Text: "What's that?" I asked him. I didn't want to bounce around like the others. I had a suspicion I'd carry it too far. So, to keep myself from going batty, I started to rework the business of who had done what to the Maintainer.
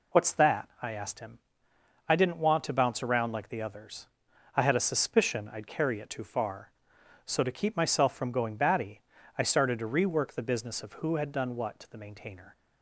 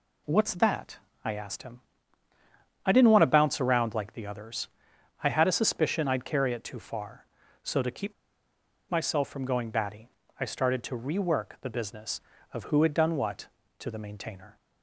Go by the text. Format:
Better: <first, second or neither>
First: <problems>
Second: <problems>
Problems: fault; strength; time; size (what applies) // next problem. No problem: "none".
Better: first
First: none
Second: pauses between "keep" and "myself"; noticeable; at 8.1 s; 0.78 s long